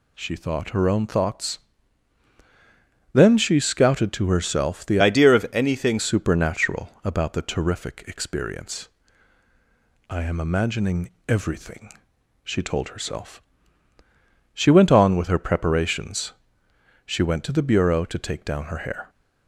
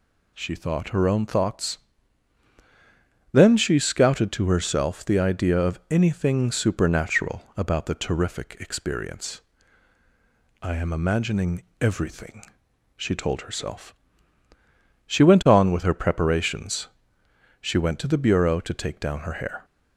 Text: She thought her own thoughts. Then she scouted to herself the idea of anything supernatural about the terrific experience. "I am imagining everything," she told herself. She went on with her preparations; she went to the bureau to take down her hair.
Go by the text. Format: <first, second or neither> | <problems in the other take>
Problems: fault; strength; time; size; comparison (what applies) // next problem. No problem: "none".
second | changes voice from "idea" to "anything"; from 4.9 to 5.9 s; 1.0 s long // pauses between "imagining" and "everything"; slight; at 11.0 s; 0.18 s long; slight in the second